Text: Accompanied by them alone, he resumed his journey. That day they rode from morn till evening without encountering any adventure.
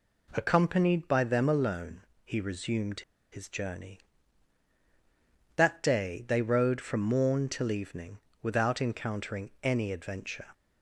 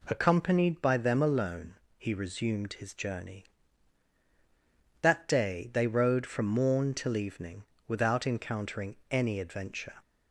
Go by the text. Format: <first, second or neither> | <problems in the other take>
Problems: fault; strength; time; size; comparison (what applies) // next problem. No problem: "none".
second | pauses between "resumed" and "his"; slight; at 3.0 s; 0.31 s long // pauses between "evening" and "without"; slight; at 8.1 s; 0.24 s long; slight in the second